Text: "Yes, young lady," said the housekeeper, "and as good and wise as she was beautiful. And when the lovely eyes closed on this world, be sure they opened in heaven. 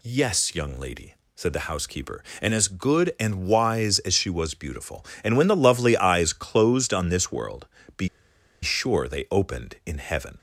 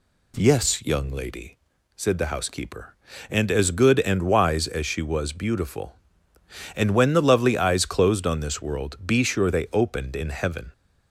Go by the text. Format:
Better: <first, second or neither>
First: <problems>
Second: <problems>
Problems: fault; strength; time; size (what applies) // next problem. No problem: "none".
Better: second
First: pauses between "be" and "sure"; noticeable; at 8.0 s; 0.55 s long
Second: none